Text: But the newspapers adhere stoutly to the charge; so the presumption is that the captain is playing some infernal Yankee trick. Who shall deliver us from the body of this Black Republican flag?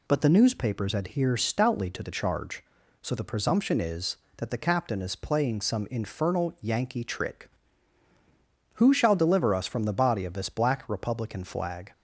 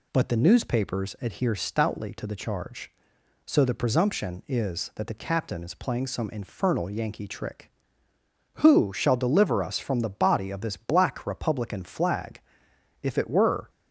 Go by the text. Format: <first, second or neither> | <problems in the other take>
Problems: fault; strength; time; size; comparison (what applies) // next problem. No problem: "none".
first | goes on to say "If it were"; noticeable; from 13.0 s on; 0.66 s long